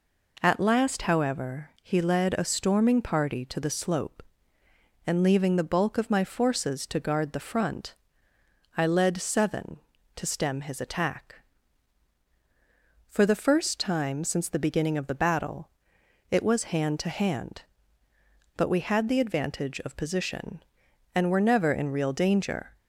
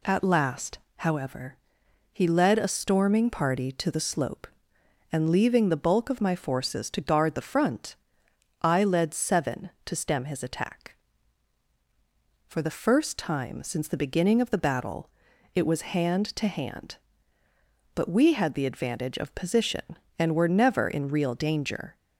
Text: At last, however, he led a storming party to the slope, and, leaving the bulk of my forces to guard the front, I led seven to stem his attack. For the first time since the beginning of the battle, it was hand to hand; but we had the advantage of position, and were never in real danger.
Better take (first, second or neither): neither